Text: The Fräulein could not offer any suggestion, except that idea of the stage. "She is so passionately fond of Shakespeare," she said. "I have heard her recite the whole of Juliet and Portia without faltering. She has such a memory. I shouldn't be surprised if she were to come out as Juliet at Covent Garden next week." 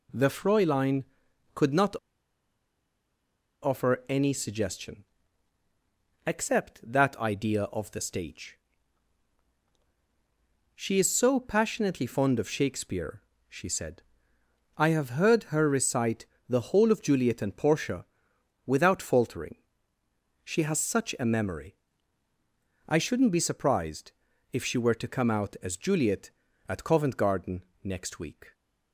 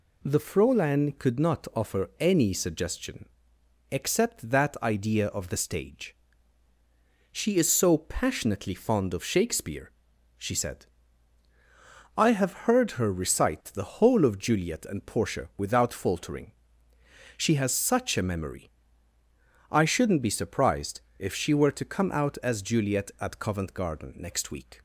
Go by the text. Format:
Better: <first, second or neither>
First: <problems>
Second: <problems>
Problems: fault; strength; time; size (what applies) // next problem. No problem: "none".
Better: second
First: pauses between "not" and "offer"; strong; at 1.9 s; 1.6 s long // pauses between "recite" and "the"; slight; at 16.2 s; 0.22 s long // pauses between "Portia" and "without"; noticeable; at 18.0 s; 0.62 s long // pauses between "surprised" and "if"; at 24.1 s; 0.40 s long // pauses between "Garden" and "next"; slight; at 27.6 s; 0.20 s long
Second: pauses between "surprised" and "if"; slight; at 21.0 s; 0.16 s long